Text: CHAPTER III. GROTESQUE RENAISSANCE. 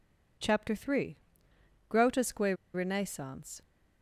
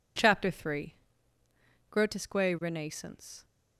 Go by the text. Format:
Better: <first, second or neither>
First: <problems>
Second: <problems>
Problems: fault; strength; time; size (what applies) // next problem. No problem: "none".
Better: second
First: pauses between "GROTESQUE" and "RENAISSANCE"; slight; at 2.5 s; 0.18 s long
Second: none